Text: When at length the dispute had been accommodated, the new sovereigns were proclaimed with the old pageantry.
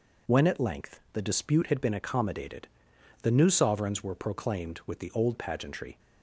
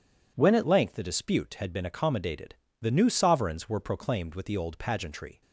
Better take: first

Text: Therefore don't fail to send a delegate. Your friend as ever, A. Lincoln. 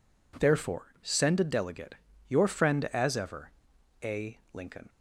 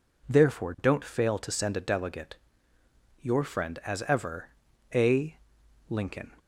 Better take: second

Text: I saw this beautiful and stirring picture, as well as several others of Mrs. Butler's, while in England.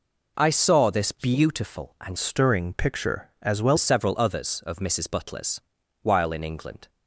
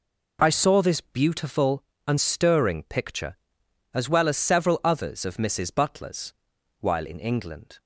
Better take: second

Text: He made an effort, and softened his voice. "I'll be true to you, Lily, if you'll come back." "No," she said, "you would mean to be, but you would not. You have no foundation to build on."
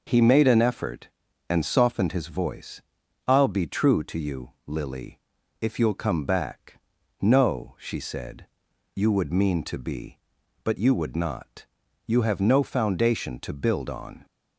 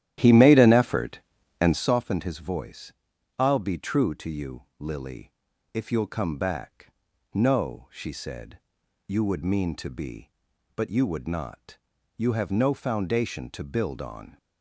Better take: first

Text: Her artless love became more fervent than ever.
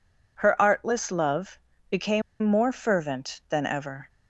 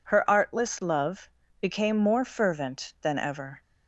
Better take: second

